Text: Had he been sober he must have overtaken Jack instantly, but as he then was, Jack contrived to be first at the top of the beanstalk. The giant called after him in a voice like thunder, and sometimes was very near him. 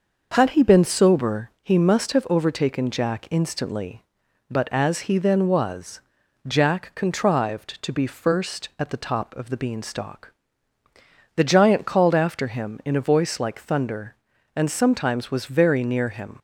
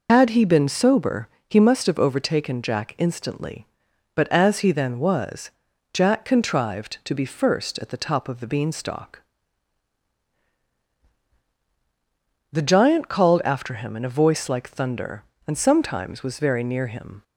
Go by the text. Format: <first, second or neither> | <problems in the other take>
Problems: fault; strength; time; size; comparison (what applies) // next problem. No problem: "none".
first | loses the start of "Had"; at 0.0 s; 80 ms // pauses between "sober" and "he"; slight; at 1.2 s; 0.18 s long